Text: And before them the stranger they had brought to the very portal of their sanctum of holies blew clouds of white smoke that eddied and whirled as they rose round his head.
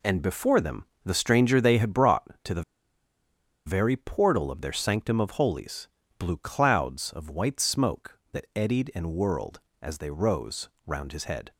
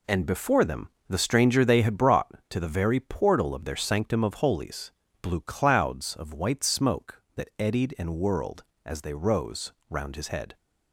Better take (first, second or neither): second